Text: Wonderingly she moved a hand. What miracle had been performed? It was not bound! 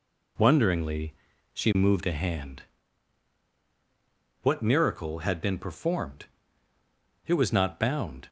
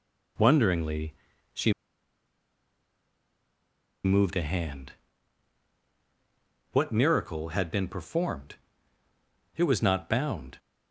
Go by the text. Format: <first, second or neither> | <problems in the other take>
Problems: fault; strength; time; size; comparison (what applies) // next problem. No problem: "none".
first | pauses between "Wonderingly" and "she"; at 1.1 s; 0.38 s long; also in the first // pauses between "she" and "moved"; strong; at 1.7 s; 2.3 s long